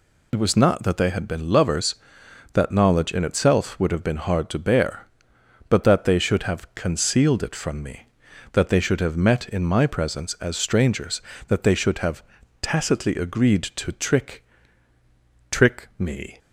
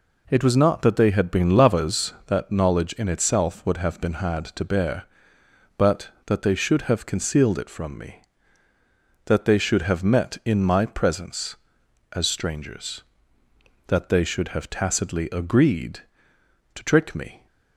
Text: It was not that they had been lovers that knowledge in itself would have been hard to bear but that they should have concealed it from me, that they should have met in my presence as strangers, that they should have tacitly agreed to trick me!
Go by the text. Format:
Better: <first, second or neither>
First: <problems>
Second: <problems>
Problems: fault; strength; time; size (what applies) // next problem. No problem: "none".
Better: second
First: pauses between "have" and "tacitly"; at 12.2 s; 0.40 s long // says "trick" twice; at 15.5 s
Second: none